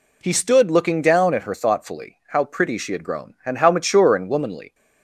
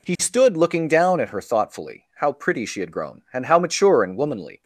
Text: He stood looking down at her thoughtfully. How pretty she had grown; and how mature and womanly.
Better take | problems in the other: neither | none

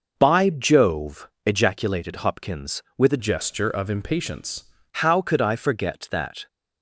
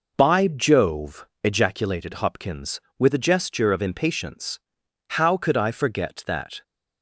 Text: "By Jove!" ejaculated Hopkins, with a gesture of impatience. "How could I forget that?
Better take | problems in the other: second | changes voice from "gesture" to "impatience"; from 3.1 to 4.6 s; 1.5 s long

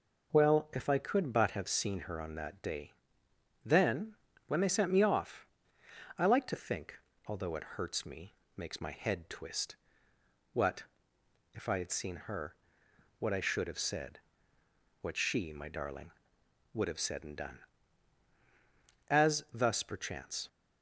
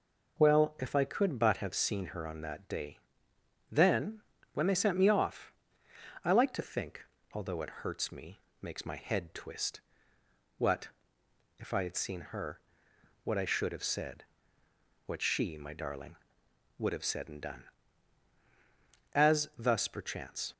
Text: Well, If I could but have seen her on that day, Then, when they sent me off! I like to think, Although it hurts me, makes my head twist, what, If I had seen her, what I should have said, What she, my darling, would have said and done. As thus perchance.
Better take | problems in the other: neither | none

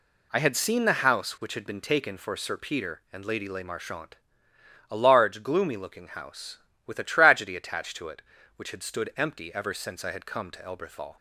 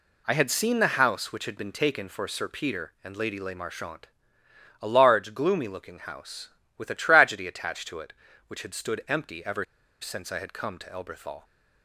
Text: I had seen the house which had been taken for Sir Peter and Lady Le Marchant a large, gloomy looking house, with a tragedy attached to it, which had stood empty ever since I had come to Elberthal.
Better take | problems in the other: first | pauses between "Marchant" and "a"; noticeable; at 4.0 s; 0.74 s long; noticeable in the first // pauses between "ever" and "since"; at 9.6 s; 0.37 s long

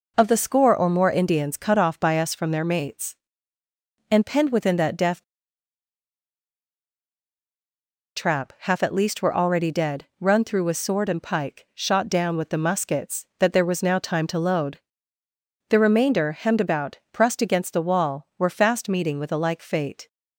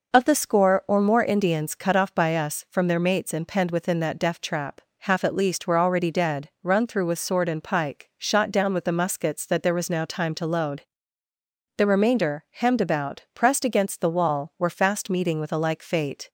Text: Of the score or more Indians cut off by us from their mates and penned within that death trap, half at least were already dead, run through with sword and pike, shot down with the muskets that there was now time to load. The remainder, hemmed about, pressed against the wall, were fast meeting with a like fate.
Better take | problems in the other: second | pauses between "death" and "trap"; strong; at 5.2 s; 2.9 s long

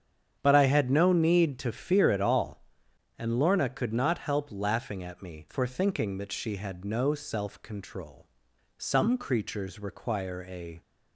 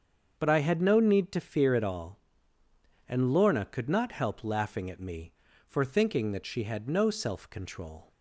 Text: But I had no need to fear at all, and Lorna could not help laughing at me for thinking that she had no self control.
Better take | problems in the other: second | starts louder than the rest; strong; until 1.4 s; 8 dB; also in the second // goes on to say "Some creatures require a"; strong; from 8.7 s on; 2.0 s long

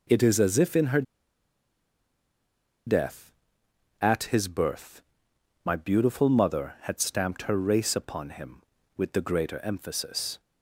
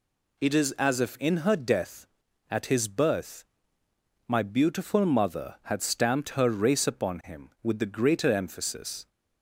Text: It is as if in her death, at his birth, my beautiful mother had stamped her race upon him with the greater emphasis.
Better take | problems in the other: second | pauses between "her" and "death"; strong; at 1.0 s; 1.8 s long

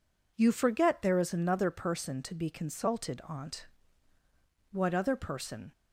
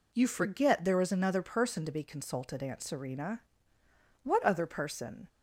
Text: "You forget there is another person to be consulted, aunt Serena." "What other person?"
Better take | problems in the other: second | skips "Serena"; at 4.1 s

